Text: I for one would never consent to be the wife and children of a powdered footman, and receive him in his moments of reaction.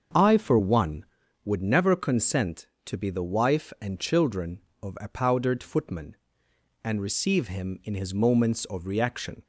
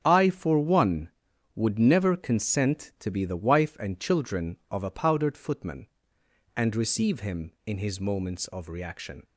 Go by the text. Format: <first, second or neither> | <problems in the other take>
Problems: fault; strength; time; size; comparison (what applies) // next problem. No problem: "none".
neither | starts louder than the rest; the same in both